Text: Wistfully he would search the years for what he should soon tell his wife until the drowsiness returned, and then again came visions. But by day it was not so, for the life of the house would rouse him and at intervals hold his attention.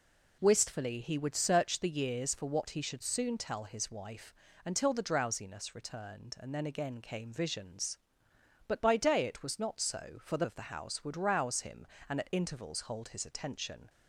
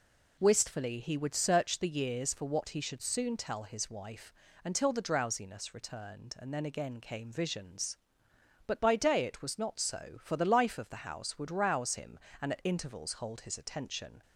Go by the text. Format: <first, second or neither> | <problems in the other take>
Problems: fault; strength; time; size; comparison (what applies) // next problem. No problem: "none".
second | pauses between "wife" and "until"; slight; at 4.3 s; 0.32 s long; slight in the second // skips "life"; at 10.4 s